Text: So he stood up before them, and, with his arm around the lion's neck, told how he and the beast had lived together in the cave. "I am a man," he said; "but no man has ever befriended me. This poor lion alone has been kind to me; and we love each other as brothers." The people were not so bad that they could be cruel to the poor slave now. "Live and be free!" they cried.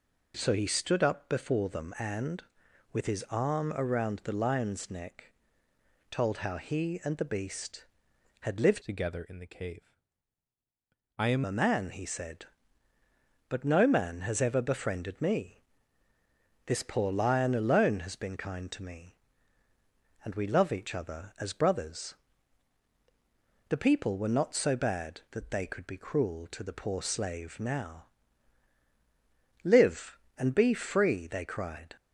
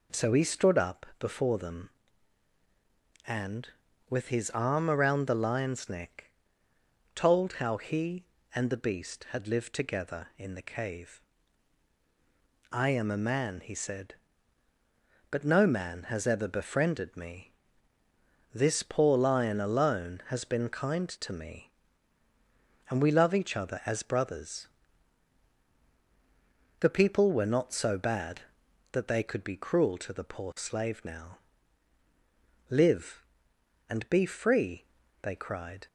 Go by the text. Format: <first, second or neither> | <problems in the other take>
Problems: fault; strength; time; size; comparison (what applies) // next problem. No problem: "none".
second | changes voice from "together" to "am"; from 8.8 to 11.4 s; 2.6 s long